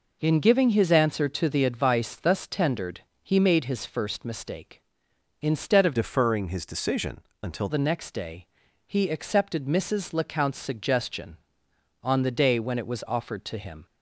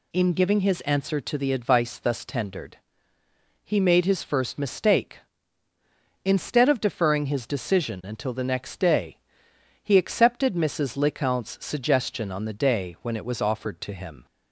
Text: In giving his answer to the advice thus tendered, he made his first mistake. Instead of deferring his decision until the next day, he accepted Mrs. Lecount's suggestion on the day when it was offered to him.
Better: second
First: changes voice from "deferring" to "until"; from 5.9 to 7.6 s; 1.7 s long // pauses between "decision" and "until"; slight; at 7.1 s; 0.26 s long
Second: none

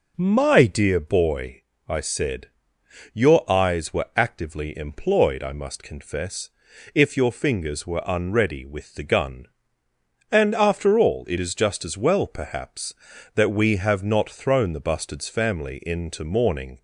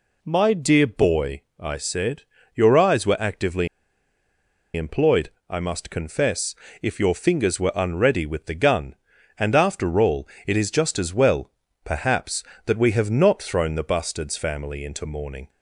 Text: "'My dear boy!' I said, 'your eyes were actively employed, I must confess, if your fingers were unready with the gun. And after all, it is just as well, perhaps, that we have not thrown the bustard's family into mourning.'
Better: first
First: none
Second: pauses between "actively" and "employed"; at 3.6 s; 1.0 s long

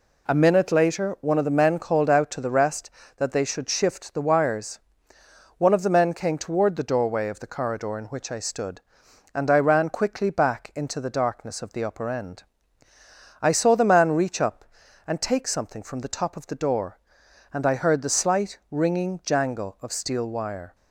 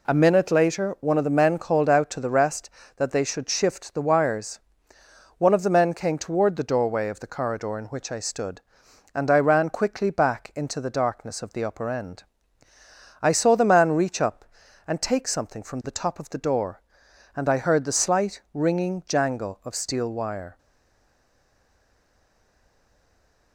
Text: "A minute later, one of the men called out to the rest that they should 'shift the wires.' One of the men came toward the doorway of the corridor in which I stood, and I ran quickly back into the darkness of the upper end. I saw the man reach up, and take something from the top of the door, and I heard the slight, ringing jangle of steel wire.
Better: first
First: none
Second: stays silent after the last word; strong; from 20.5 s on; 3.0 s long

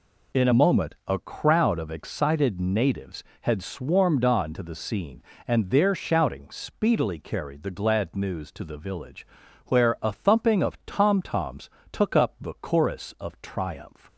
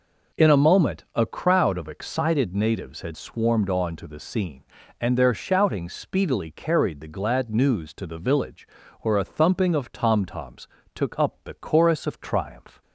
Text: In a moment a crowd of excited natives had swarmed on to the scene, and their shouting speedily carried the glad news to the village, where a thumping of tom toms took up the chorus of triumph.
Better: neither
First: pauses between "toms" and "took"; slight; at 11.6 s; 0.24 s long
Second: pauses between "toms" and "took"; slight; at 10.6 s; 0.26 s long

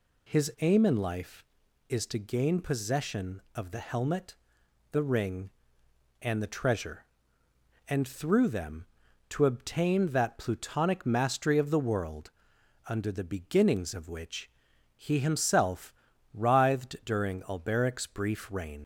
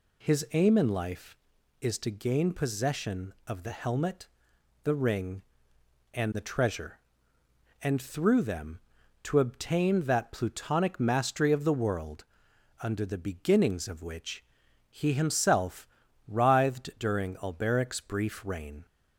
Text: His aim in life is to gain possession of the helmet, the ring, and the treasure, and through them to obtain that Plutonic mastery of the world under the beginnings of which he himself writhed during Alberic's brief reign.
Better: second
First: pauses between "world" and "under"; noticeable; at 12.2 s; 0.58 s long // pauses between "which" and "he"; at 14.5 s; 0.44 s long // pauses between "himself" and "writhed"; at 15.9 s; 0.40 s long // leaves "reign" unfinished; at 18.8 s; 70 ms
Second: pauses between "world" and "under"; noticeable; at 12.2 s; 0.58 s long // pauses between "which" and "he"; at 14.4 s; 0.44 s long // pauses between "himself" and "writhed"; at 15.8 s; 0.40 s long

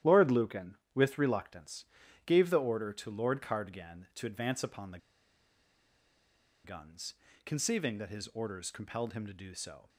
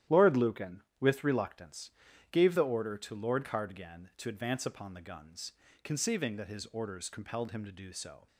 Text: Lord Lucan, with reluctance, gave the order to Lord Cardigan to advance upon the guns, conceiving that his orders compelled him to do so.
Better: second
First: starts louder than the rest; strong; until 1.2 s; 11.5 dB // pauses between "the" and "guns"; strong; at 4.9 s; 1.6 s long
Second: starts louder than the rest; strong; until 1.3 s; 11.5 dB

